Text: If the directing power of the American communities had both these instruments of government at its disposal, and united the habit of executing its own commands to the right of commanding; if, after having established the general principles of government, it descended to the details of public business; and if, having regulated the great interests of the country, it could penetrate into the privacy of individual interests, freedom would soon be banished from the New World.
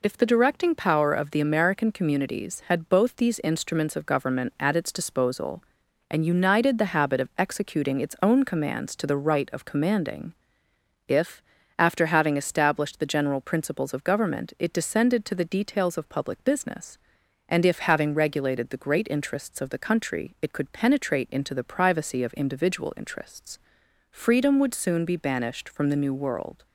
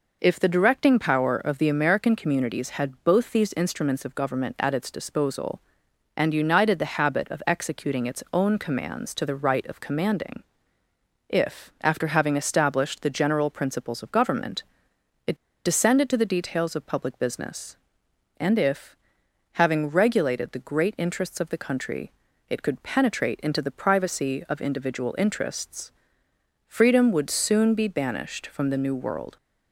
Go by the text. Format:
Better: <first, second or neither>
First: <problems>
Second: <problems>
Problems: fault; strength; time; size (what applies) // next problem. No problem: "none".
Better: first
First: none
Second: pauses between "it" and "descended"; slight; at 15.3 s; 0.29 s long